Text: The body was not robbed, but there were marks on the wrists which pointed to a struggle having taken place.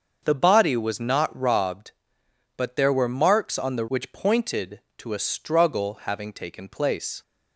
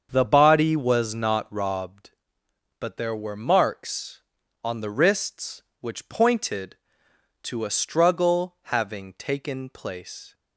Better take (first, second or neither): second